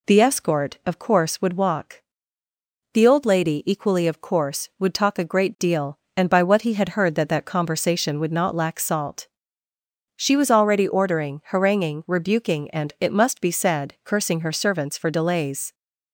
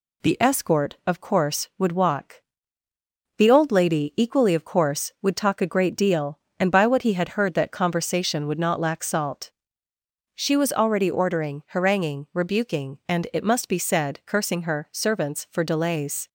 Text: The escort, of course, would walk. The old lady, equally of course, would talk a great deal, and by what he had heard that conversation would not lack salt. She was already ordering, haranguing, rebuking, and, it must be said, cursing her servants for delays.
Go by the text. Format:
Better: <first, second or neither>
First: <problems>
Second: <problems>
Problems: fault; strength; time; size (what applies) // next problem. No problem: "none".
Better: second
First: says "that" twice; at 7.2 s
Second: none